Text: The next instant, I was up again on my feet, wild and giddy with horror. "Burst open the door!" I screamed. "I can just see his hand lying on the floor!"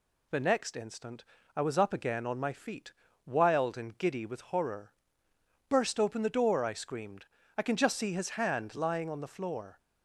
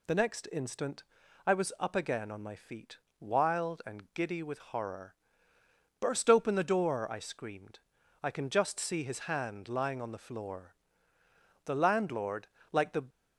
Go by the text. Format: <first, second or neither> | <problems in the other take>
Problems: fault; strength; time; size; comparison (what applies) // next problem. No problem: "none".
first | goes on to say "The landlord like the"; from 11.6 s on; 1.4 s long